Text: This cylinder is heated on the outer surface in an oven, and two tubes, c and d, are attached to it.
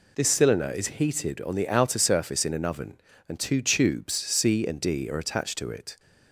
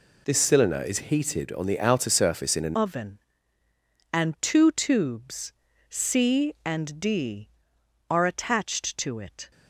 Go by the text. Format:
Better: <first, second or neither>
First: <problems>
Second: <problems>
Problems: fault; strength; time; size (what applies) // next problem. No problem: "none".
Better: first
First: none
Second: changes voice at "oven"; from 2.7 s on; 6.8 s long